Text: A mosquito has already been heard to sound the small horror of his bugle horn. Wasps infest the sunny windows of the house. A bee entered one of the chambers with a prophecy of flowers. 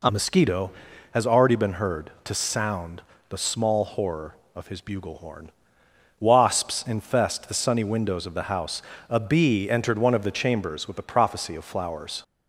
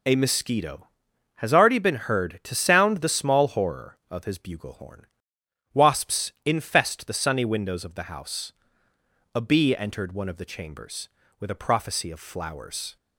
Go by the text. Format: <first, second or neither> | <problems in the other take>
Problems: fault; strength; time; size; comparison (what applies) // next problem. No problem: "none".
second | changes voice at "mosquito"; from 0.1 s on; 12.1 s long // pauses between "sound" and "the"; slight; at 3.0 s; 0.28 s long